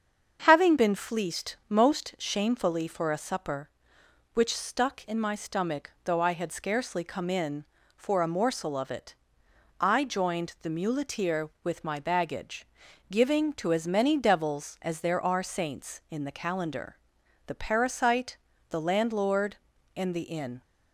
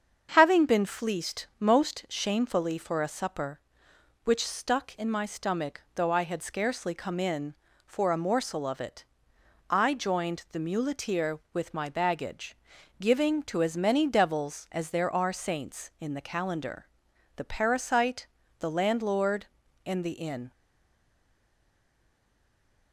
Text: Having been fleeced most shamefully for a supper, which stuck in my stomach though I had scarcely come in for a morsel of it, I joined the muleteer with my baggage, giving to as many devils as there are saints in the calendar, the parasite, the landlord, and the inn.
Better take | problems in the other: first | starts louder than the rest; until 1.3 s; 7 dB; also in the first // stays silent after the last word; from 20.5 s on; 2.4 s long

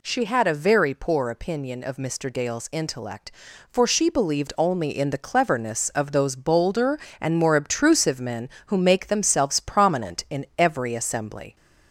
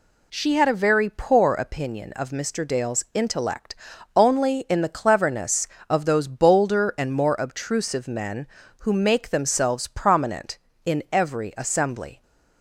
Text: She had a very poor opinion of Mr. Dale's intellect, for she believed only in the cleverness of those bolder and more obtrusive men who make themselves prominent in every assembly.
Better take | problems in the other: first | skips "for she believed"; at 3.9 s

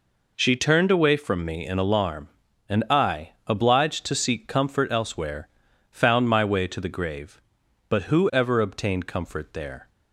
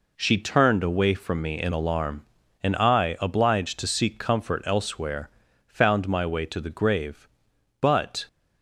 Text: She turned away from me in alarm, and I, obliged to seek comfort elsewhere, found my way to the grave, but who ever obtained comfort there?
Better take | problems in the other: first | stops before "who ever obtained comfort there"; at 8.2 s

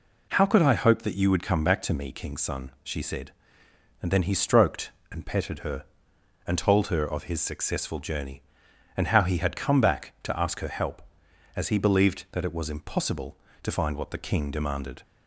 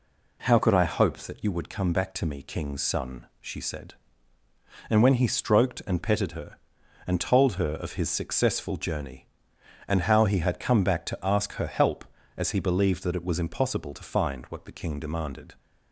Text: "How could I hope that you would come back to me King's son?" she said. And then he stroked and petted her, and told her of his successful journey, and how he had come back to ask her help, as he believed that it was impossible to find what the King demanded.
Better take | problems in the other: first | says "when" for "then"; at 5.0 s

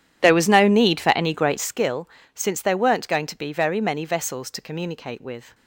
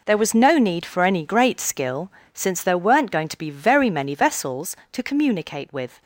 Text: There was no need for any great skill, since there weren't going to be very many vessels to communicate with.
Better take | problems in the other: second | starts louder than the rest; strong; until 1.9 s; 10.5 dB

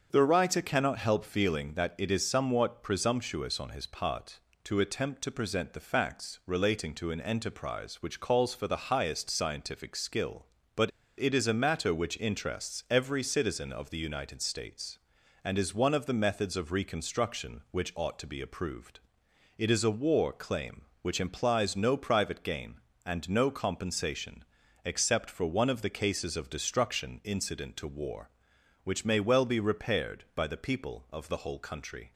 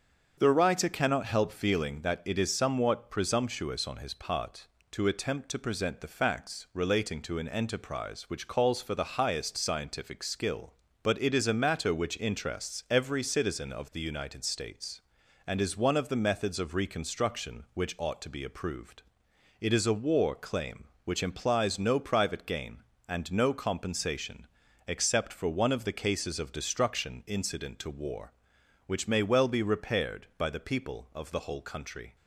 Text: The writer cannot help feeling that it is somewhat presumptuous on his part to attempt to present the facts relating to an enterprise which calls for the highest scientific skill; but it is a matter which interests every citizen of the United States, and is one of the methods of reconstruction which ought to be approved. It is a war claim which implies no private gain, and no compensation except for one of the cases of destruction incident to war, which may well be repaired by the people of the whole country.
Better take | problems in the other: second | starts louder than the rest; until 1.1 s; 7 dB; also in the second // pauses between "but" and "it"; slight; at 10.9 s; 0.30 s long // pauses between "compensation" and "except"; at 24.4 s; 0.40 s long; also in the second

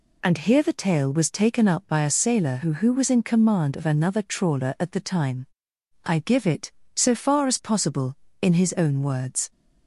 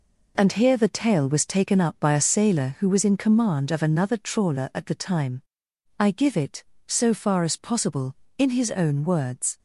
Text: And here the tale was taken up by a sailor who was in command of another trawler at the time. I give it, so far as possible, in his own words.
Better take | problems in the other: second | says "who" twice; at 2.7 s

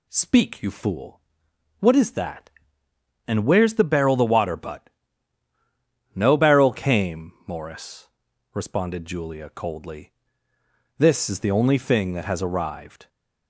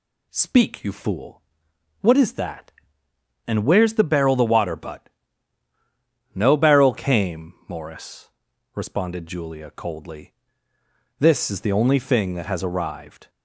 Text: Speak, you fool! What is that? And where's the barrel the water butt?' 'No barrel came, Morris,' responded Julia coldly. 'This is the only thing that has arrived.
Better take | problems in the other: neither | none

